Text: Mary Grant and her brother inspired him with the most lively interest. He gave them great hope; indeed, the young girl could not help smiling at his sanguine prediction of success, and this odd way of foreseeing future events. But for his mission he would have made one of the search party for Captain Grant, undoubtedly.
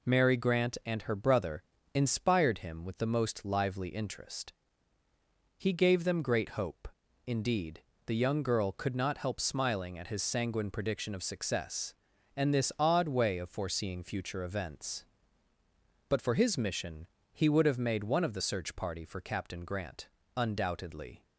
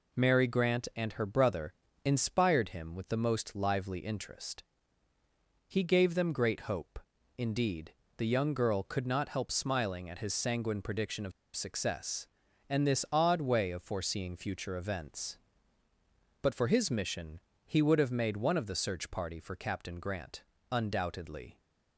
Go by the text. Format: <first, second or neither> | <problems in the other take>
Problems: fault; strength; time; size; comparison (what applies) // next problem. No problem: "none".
first | pauses between "brother" and "inspired"; slight; at 1.7 s; 0.32 s long; slight in the first // pauses between "of" and "success"; slight; at 11.3 s; 0.24 s long // pauses between "mission" and "he"; slight; at 17.3 s; 0.24 s long; slight in the first